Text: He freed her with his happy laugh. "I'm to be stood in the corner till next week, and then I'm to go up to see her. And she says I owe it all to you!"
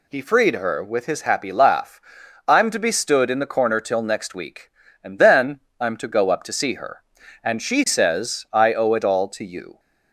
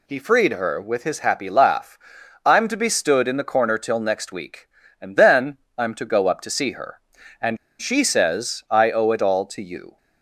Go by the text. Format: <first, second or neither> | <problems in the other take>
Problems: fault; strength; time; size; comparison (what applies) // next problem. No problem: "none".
first | pauses between "then" and "I'm"; slight; at 5.5 s; 0.20 s long; slight in the first // pauses between "And" and "she"; slight; at 7.5 s; 0.23 s long